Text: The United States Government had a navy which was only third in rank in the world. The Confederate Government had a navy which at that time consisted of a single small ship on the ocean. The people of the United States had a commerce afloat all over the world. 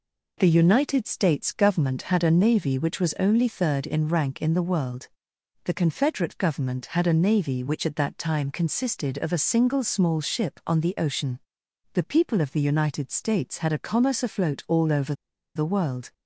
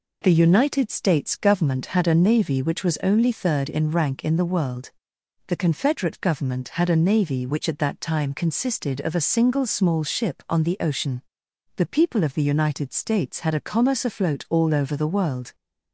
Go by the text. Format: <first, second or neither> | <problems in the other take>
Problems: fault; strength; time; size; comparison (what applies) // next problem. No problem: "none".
second | pauses between "over" and "the"; at 15.1 s; 0.42 s long